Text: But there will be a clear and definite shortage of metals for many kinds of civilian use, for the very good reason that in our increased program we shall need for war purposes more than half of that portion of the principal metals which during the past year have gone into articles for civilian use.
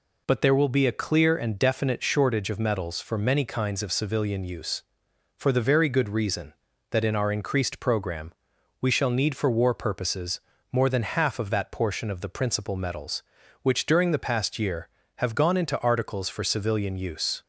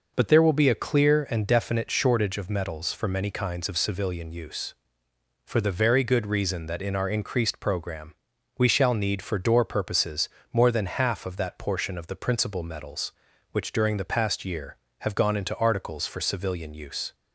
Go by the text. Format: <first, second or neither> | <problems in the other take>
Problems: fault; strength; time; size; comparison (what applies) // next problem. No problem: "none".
first | pauses between "program" and "we"; at 8.1 s; 0.42 s long; noticeable in the first // says "door" for "war"; at 9.3 s // pauses between "purposes" and "more"; slight; at 10.2 s; 0.24 s long; slight in the first